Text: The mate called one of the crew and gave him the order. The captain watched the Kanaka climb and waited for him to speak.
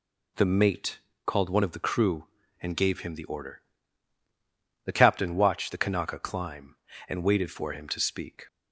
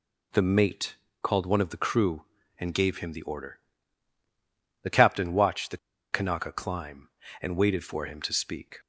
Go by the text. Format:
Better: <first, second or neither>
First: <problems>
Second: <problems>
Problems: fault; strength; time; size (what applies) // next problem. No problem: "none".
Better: first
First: pauses between "mate" and "called"; slight; at 0.9 s; 0.28 s long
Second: pauses between "mate" and "called"; slight; at 0.9 s; 0.28 s long // pauses between "the" and "Kanaka"; slight; at 5.7 s; 0.35 s long